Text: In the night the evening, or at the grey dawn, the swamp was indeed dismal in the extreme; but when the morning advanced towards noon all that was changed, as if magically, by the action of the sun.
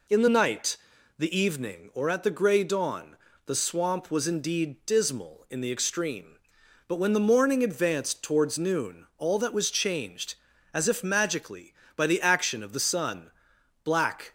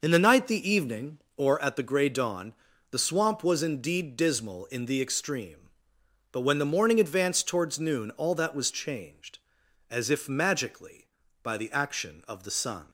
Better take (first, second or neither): second